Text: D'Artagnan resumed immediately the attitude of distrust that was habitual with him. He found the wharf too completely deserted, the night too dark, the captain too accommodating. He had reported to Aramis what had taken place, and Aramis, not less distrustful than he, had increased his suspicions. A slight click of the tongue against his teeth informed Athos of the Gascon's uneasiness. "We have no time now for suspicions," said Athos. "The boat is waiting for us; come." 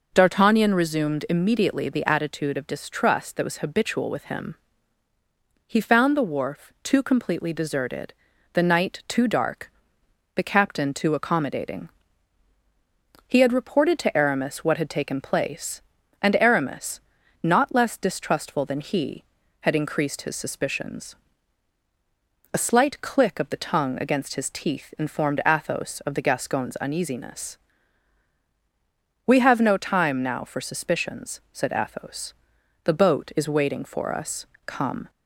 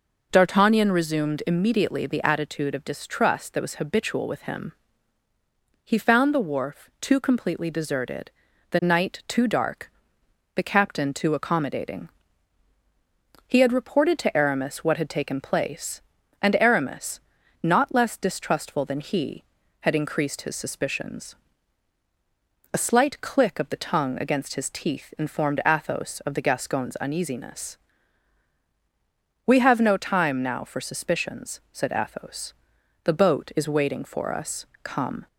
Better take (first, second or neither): neither